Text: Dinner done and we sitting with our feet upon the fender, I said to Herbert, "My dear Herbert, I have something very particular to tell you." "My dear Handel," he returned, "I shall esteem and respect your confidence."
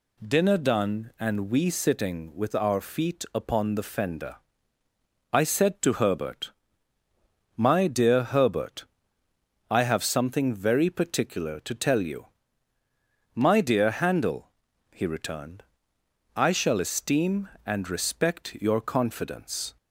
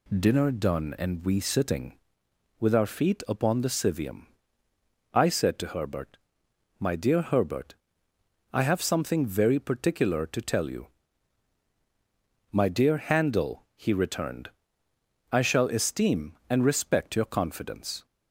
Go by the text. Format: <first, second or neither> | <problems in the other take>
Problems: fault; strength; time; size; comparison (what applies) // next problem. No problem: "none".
first | says "civium" for "fender"; at 3.6 s